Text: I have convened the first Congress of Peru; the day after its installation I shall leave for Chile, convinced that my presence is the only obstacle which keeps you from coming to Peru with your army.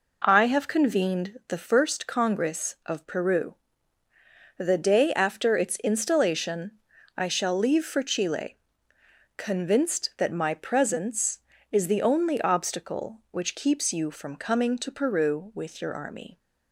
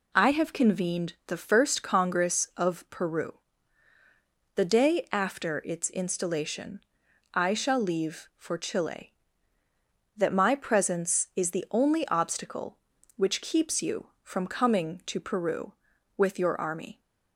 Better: first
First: pauses between "installation" and "I"; noticeable; at 6.7 s; 0.46 s long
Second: pauses between "installation" and "I"; noticeable; at 6.8 s; 0.52 s long // skips "convinced"; at 9.6 s

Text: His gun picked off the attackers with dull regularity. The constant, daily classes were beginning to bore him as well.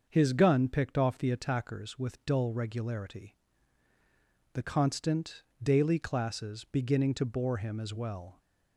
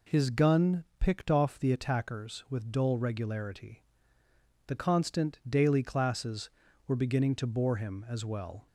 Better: second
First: starts louder than the rest; until 1.1 s; 6.5 dB // skips "were"; at 6.6 s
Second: none

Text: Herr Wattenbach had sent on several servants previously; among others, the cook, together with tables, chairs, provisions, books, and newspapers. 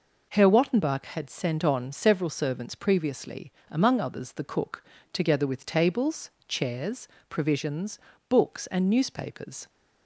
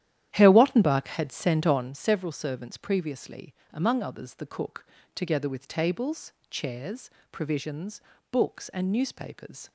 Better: first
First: none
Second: starts louder than the rest; strong; until 2.0 s; 11 dB

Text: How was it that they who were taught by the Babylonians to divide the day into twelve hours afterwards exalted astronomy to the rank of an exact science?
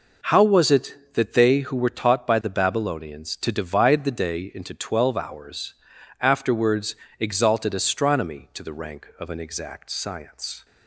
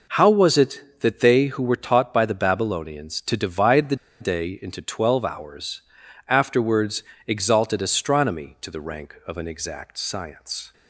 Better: first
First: pauses between "hours" and "afterwards"; noticeable; at 5.7 s; 0.46 s long // pauses between "afterwards" and "exalted"; slight; at 6.9 s; 0.24 s long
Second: pauses between "the" and "day"; slight; at 3.9 s; 0.24 s long // pauses between "hours" and "afterwards"; noticeable; at 5.8 s; 0.46 s long // pauses between "afterwards" and "exalted"; slight; at 7.0 s; 0.24 s long

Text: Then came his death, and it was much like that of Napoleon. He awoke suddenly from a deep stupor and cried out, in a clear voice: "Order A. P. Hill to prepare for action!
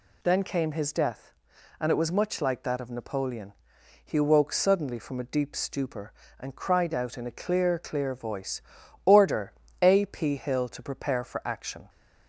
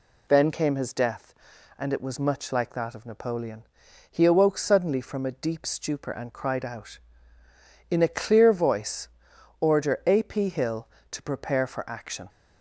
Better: second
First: says "clear" twice; at 7.7 s // pauses between "Order" and "A"; slight; at 9.5 s; 0.28 s long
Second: none

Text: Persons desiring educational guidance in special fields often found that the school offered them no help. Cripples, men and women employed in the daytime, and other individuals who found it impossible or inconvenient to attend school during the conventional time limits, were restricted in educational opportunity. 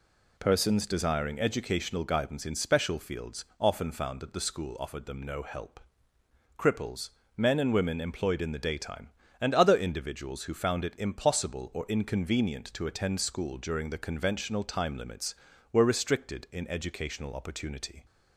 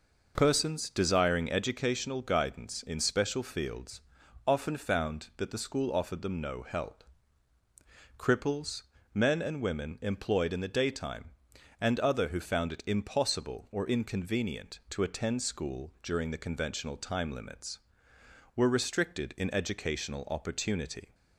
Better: first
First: pauses between "fields" and "often"; slight; at 3.4 s; 0.16 s long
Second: pauses between "fields" and "often"; at 4.0 s; 0.44 s long // skips "individuals"; at 12.2 s

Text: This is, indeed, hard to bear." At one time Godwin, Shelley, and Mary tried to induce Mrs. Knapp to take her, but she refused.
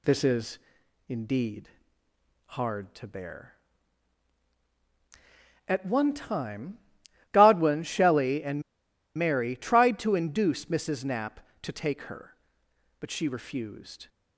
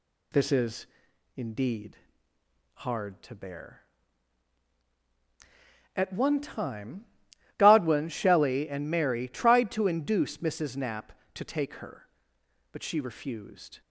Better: second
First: pauses between "time" and "Godwin"; noticeable; at 6.7 s; 0.54 s long // pauses between "and" and "Mary"; noticeable; at 8.6 s; 0.54 s long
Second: pauses between "time" and "Godwin"; noticeable; at 7.0 s; 0.54 s long

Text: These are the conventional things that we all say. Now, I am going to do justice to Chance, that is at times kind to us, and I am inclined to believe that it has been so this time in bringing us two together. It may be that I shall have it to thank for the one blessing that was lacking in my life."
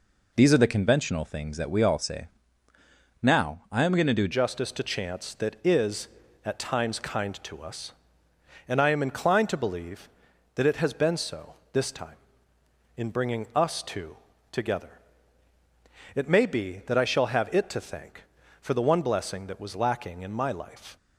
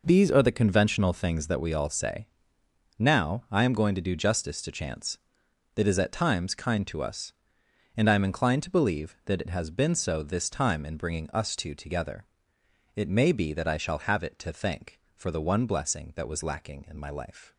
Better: second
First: changes voice at "justice"; from 4.3 s on; 16.6 s long // pauses between "so" and "this"; slight; at 11.5 s; 0.20 s long // pauses between "two" and "together"; slight; at 14.1 s; 0.36 s long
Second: none

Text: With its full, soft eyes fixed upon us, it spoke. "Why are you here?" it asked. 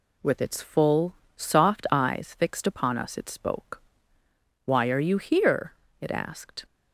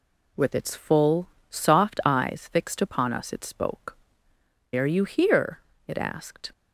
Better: first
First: none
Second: skips "Why"; at 4.3 s

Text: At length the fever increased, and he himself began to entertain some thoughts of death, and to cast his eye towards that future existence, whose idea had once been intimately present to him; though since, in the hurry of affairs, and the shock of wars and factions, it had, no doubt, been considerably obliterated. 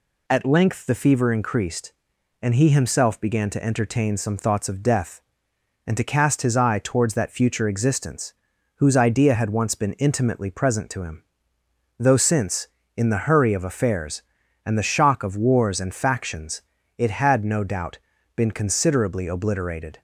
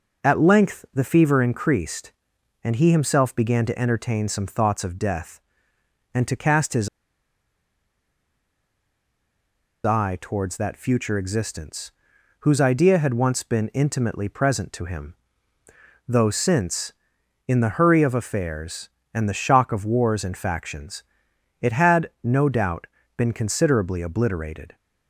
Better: first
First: none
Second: pauses between "his" and "eye"; strong; at 6.8 s; 2.9 s long

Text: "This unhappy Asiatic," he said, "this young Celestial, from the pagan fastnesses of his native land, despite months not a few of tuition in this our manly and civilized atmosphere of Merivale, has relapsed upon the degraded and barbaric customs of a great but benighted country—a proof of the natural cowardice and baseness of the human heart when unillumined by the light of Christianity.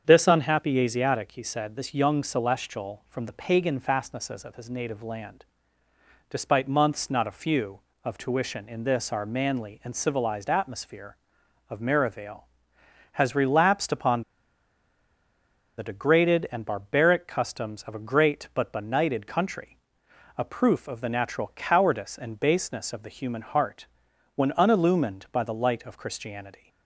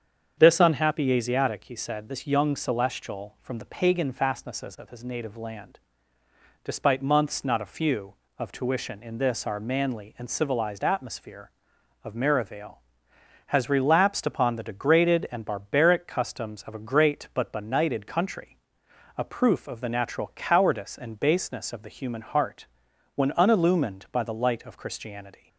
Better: second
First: starts louder than the rest; strong; until 1.0 s; 7.5 dB // pauses between "upon" and "the"; strong; at 14.2 s; 1.5 s long // pauses between "heart" and "when"; noticeable; at 23.8 s; 0.48 s long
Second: starts louder than the rest; strong; until 1.3 s; 7.5 dB // pauses between "heart" and "when"; noticeable; at 22.6 s; 0.48 s long

